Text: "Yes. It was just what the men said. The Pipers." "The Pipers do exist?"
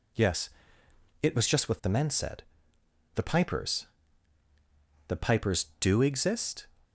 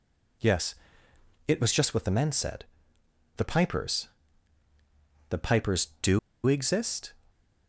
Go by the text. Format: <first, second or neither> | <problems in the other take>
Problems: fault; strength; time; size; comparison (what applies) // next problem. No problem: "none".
first | pauses between "do" and "exist"; slight; at 6.1 s; 0.27 s long